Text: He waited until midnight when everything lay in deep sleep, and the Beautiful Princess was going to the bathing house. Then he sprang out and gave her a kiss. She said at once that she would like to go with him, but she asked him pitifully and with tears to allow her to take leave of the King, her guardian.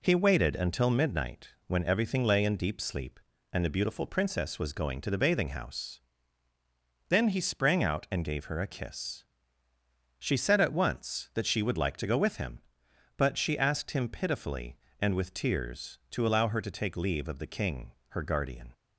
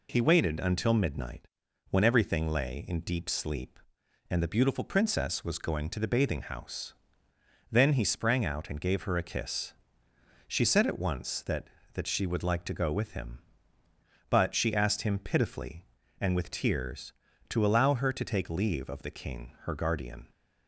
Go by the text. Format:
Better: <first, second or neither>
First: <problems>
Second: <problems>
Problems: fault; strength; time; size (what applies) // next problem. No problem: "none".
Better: first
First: pauses between "midnight" and "when"; slight; at 1.5 s; 0.16 s long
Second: pauses between "midnight" and "when"; at 1.4 s; 0.44 s long // says "that" twice; at 11.9 s